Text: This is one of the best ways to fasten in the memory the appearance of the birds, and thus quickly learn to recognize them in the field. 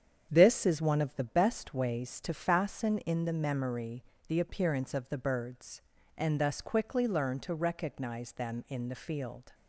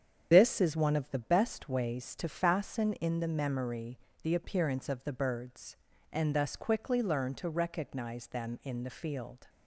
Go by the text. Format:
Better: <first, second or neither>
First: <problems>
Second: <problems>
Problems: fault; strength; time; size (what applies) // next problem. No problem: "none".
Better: first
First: starts louder than the rest; strong; until 1.3 s; 8 dB // pauses between "memory" and "the"; slight; at 4.0 s; 0.24 s long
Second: loses the start of "This"; at 0.3 s; 65 ms // starts louder than the rest; strong; until 1.3 s; 8 dB // pauses between "memory" and "the"; slight; at 3.9 s; 0.24 s long